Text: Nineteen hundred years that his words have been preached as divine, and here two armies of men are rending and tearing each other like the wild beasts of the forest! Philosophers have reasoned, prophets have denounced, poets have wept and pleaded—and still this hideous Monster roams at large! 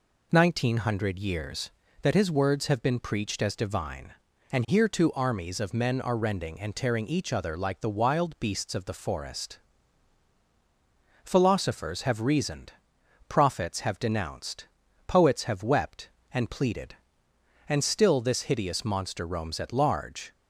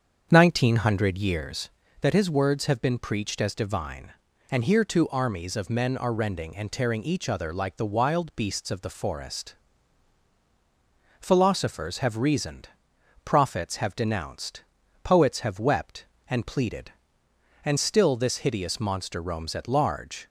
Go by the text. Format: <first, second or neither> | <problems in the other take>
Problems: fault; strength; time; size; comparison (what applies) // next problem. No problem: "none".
first | starts louder than the rest; strong; until 1.5 s; 7.5 dB